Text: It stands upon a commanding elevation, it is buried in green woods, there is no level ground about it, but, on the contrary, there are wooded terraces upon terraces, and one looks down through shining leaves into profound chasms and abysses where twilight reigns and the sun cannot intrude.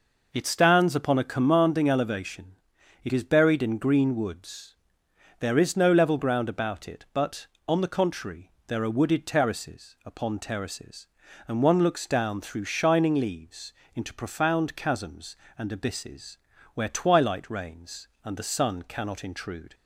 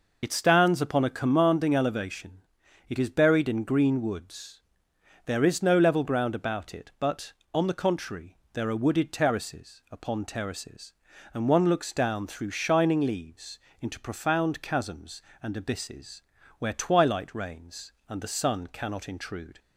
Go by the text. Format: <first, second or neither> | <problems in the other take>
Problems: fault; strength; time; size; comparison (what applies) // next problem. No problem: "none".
first | loses the start of "It"; at 0.2 s; 40 ms // pauses between "leaves" and "into"; slight; at 13.5 s; 0.24 s long; slight in the first // pauses between "abysses" and "where"; at 16.2 s; 0.38 s long; also in the first